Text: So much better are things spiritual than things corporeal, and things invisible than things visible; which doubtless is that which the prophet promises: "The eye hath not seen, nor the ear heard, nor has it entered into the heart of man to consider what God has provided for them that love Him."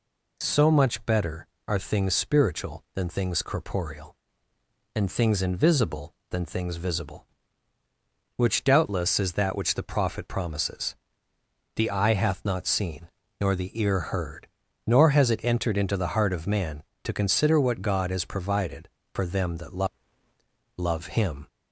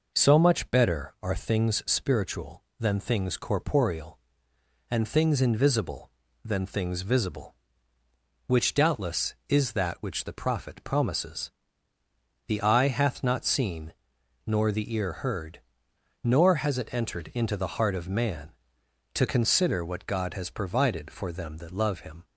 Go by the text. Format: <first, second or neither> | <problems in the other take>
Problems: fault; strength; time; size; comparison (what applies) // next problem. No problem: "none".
second | says "love" twice; at 20.7 s